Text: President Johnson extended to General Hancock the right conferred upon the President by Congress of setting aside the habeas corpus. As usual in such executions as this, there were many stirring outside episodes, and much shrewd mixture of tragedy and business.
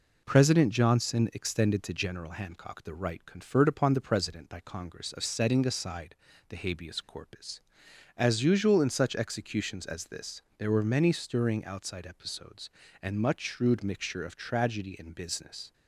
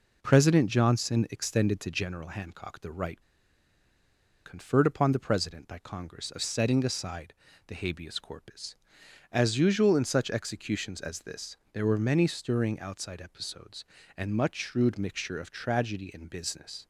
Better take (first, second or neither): first